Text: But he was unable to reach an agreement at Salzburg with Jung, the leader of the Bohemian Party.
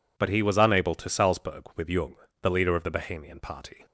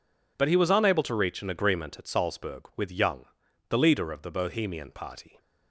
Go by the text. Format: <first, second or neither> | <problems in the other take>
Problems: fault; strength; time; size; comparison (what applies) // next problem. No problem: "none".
second | skips "reach an agreement at"; at 1.0 s